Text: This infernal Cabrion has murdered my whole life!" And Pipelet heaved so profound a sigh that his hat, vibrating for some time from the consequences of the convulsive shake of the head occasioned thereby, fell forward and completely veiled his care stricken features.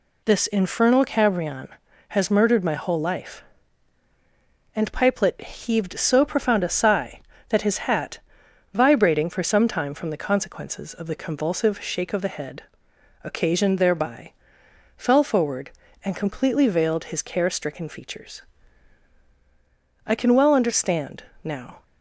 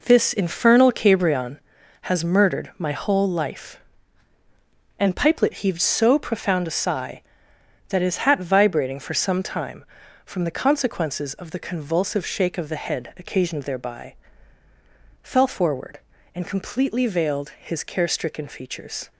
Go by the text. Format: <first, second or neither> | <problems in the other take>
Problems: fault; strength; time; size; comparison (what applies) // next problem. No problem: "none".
second | pauses between "head" and "occasioned"; noticeable; at 12.6 s; 0.62 s long // goes on to say "I can well understand now"; strong; from 20.0 s on; 1.7 s long